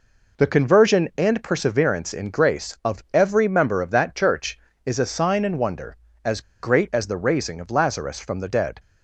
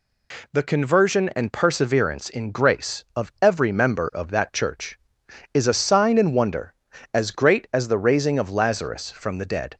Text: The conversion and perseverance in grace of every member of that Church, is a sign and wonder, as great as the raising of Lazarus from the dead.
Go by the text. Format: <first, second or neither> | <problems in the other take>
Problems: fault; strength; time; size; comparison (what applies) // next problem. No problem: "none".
second | pauses between "as" and "great"; slight; at 6.4 s; 0.21 s long